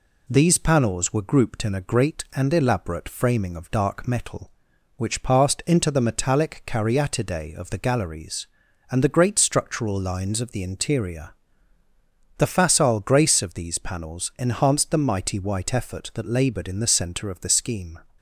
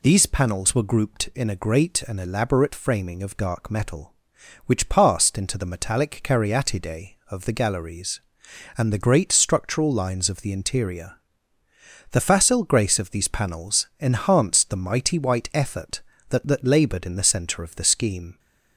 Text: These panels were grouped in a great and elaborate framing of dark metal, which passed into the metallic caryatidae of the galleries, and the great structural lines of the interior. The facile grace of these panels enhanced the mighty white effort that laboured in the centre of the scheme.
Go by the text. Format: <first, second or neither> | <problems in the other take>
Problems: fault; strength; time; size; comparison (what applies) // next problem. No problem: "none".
first | says "that" twice; at 16.4 s